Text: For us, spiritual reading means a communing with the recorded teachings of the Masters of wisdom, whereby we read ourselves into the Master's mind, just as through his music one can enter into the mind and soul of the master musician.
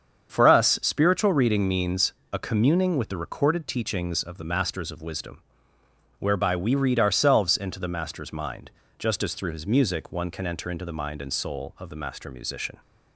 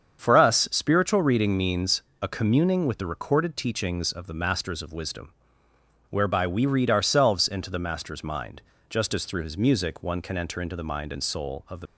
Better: first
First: starts louder than the rest; strong; until 1.3 s; 7.5 dB // pauses between "means" and "a"; slight; at 2.1 s; 0.18 s long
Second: starts louder than the rest; strong; until 1.2 s; 7.5 dB // pauses between "means" and "a"; slight; at 2.0 s; 0.18 s long // stops before "master musician"; at 11.8 s

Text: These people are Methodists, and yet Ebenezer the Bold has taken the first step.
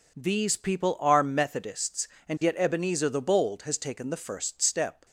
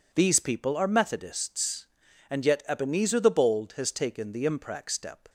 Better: first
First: none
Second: says "imprac" for "first"; at 4.4 s

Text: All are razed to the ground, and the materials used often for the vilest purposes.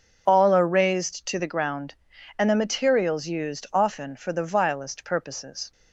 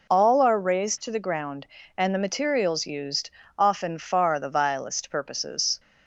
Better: first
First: none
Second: pauses between "used" and "often"; slight; at 3.3 s; 0.26 s long // says "far" for "for"; at 3.9 s

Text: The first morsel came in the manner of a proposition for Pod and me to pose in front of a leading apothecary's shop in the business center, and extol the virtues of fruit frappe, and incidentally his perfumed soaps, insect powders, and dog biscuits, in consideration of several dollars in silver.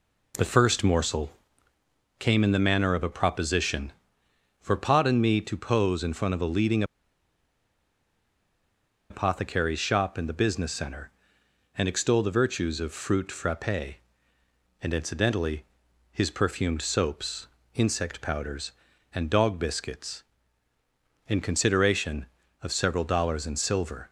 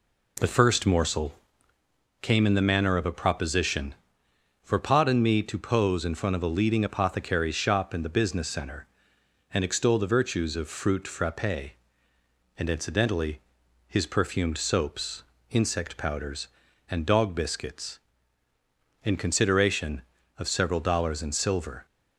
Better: second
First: pauses between "morsel" and "came"; noticeable; at 1.3 s; 0.88 s long // pauses between "leading" and "apothecary's"; strong; at 6.8 s; 2.2 s long // pauses between "incidentally" and "his"; noticeable; at 15.6 s; 0.48 s long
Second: pauses between "morsel" and "came"; noticeable; at 1.3 s; 0.88 s long // pauses between "incidentally" and "his"; noticeable; at 13.3 s; 0.48 s long

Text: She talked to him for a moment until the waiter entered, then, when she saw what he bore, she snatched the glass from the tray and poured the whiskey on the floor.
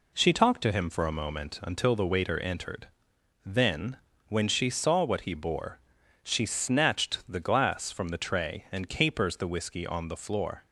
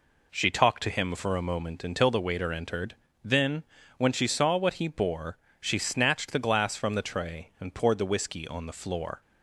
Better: second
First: says "capers" for "poured"; at 8.8 s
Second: none

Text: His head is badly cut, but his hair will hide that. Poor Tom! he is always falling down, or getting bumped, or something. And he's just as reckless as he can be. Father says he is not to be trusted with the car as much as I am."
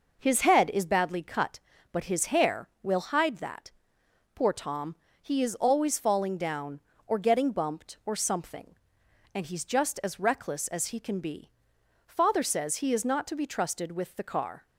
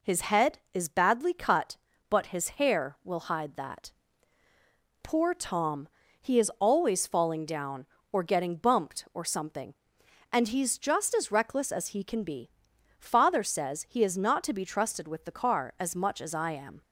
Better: second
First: stops before "as much as I am"; at 14.6 s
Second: none

